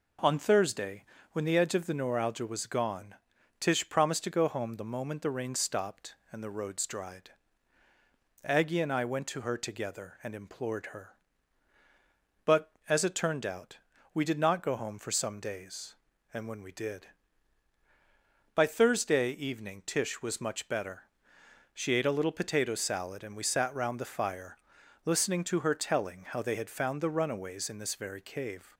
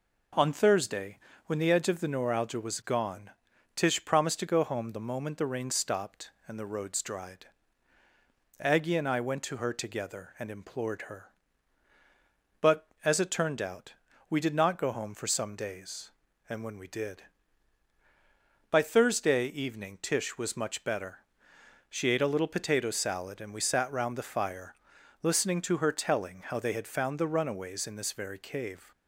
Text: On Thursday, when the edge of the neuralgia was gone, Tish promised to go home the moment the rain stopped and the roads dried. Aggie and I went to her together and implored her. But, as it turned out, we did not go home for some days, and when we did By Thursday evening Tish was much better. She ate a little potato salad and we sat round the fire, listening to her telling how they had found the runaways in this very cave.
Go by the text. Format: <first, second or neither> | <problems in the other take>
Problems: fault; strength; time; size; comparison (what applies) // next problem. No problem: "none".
neither | none